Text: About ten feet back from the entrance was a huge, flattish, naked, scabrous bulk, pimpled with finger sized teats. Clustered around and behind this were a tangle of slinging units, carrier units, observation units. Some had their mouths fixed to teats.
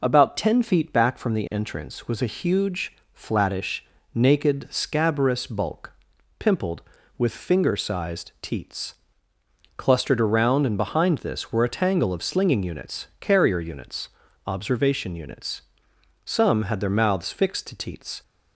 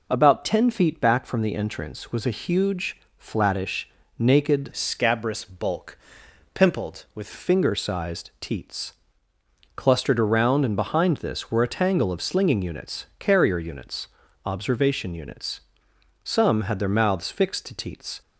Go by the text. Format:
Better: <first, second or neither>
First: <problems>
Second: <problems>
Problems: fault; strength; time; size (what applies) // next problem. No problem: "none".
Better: first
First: none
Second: changes voice from "scabrous" to "with"; from 4.7 to 7.2 s; 2.5 s long